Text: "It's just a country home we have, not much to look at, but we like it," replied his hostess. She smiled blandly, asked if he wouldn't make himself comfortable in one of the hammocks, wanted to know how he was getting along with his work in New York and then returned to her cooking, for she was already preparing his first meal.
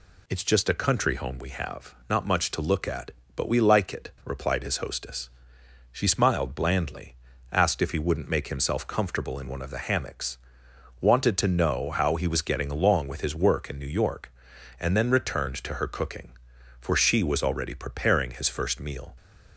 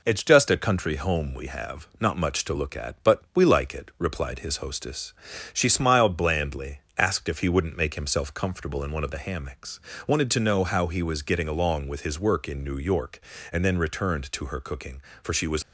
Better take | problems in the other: first | stops before "already preparing his first meal"; at 15.6 s

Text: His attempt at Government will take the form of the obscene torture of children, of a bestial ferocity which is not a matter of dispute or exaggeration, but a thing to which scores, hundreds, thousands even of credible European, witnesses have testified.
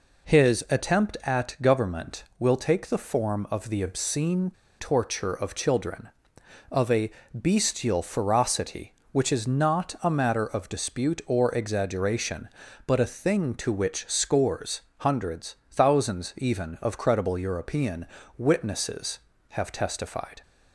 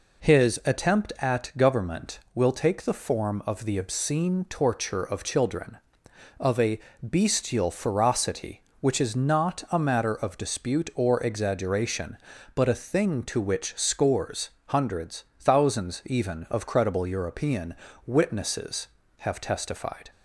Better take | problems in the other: second | pauses between "obscene" and "torture"; slight; at 4.4 s; 0.30 s long // pauses between "a" and "bestial"; slight; at 7.1 s; 0.20 s long; slight in the second

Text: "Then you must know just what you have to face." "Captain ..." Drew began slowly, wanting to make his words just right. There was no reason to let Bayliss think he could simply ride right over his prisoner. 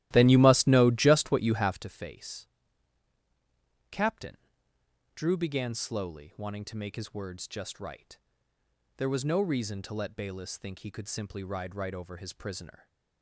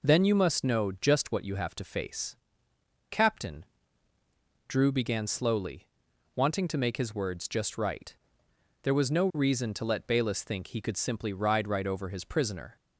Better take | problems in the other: second | starts louder than the rest; strong; until 1.8 s; 14.5 dB

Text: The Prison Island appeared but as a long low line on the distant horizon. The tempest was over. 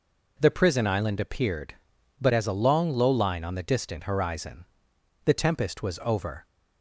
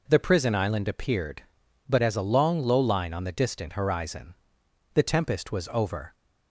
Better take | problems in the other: neither | none

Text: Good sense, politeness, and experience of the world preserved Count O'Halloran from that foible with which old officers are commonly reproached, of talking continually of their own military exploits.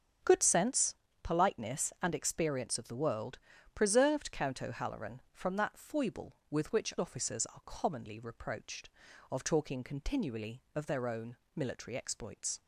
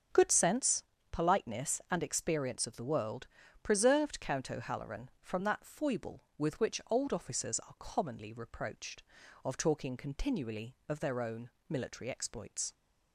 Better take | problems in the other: second | starts louder than the rest; until 1.5 s; 7 dB; also in the second // pauses between "world" and "preserved"; slight; at 3.3 s; 0.34 s long; slight in the second // skips "old"; at 6.9 s // pauses between "own" and "military"; slight; at 11.3 s; 0.18 s long; slight in the second

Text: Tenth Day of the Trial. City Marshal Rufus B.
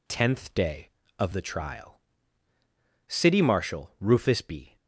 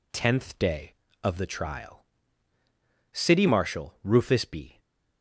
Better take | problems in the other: neither | none

